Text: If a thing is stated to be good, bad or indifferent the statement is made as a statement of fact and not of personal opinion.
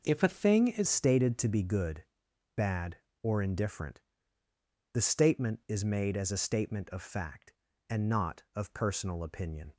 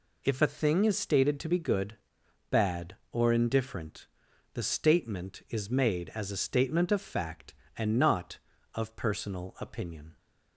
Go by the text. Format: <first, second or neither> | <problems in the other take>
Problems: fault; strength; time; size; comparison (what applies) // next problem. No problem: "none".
second | changes voice at "stated"; from 0.8 s on; 8.9 s long // pauses between "indifferent" and "the"; noticeable; at 4.0 s; 0.92 s long; noticeable in the second